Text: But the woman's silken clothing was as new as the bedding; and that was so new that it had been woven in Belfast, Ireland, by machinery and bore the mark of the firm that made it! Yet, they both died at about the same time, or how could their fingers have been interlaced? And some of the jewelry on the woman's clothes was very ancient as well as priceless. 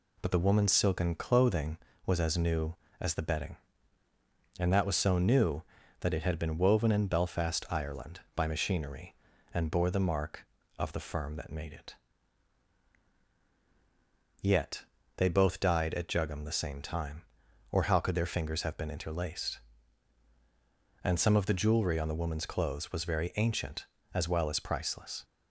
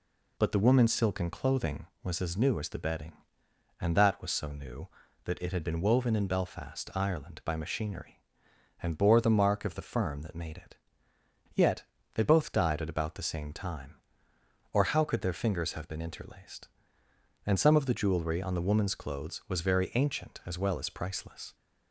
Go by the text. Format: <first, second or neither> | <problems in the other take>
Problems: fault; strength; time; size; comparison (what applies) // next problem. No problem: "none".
second | says "jugum" for "about"; at 16.0 s